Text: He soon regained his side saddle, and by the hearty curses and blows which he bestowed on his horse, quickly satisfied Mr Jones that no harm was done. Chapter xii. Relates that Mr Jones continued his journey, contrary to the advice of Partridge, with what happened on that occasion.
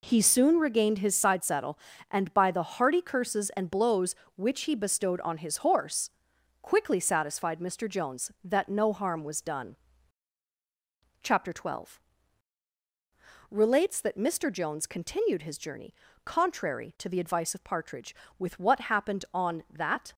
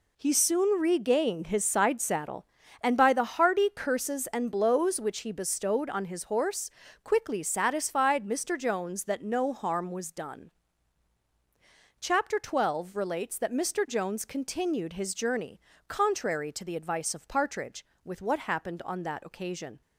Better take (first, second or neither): second